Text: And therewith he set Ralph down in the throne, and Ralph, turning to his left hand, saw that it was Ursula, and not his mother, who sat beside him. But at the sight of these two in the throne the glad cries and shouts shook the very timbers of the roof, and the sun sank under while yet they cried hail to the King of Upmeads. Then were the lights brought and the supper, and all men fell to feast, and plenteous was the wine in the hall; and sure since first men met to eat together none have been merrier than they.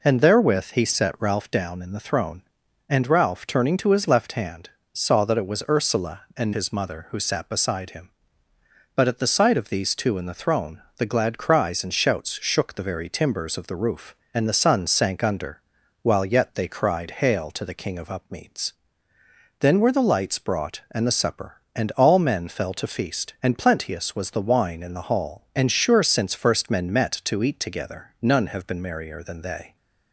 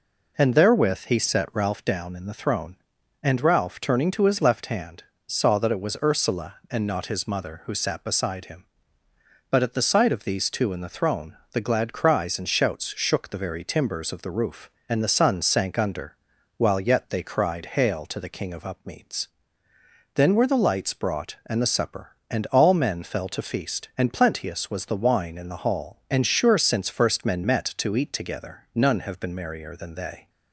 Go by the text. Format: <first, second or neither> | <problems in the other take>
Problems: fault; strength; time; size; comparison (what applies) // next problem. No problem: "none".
second | skips "not"; at 6.5 s // pauses between "throne" and "the"; slight; at 10.8 s; 0.16 s long; slight in the second // pauses between "under" and "while"; at 15.6 s; 0.40 s long; also in the second